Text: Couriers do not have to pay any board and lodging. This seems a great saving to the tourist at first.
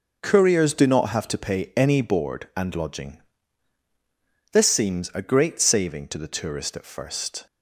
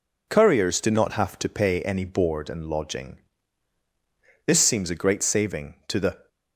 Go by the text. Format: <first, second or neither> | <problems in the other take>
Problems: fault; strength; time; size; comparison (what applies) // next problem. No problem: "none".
first | stops before "tourist at first"; at 6.2 s